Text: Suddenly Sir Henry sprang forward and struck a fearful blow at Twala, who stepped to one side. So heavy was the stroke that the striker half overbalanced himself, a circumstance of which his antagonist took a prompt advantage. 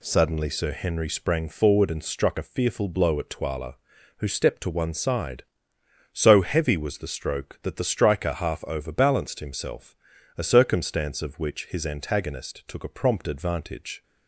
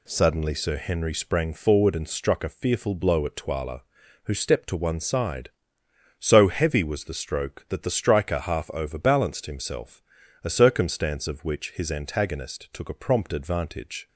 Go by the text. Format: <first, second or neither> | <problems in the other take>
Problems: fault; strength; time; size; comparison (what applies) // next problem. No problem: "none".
neither | none